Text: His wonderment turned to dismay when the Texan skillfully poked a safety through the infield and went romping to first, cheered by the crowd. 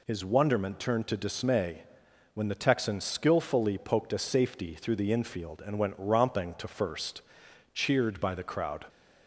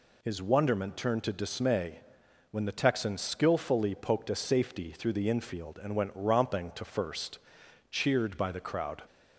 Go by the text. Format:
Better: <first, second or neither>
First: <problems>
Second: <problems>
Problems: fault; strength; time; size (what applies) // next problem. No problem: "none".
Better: neither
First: pauses between "dismay" and "when"; noticeable; at 1.8 s; 0.52 s long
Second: pauses between "dismay" and "when"; noticeable; at 1.9 s; 0.52 s long